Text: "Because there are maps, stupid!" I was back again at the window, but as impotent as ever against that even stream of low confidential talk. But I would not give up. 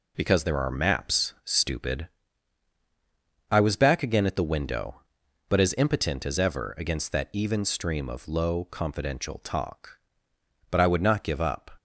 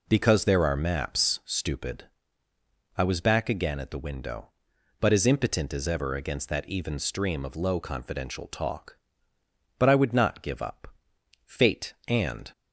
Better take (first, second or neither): first